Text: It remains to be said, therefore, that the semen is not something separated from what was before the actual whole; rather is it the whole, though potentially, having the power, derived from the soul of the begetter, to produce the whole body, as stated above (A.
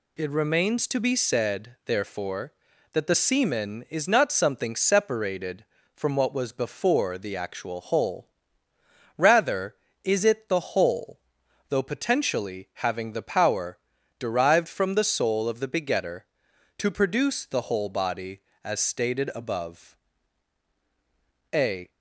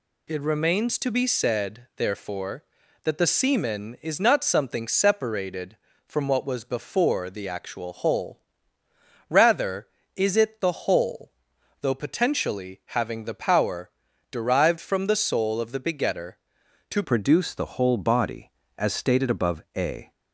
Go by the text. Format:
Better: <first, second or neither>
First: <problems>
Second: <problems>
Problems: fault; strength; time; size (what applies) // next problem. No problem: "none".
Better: first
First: none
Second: changes voice at "produce"; from 17.0 s on; 3.1 s long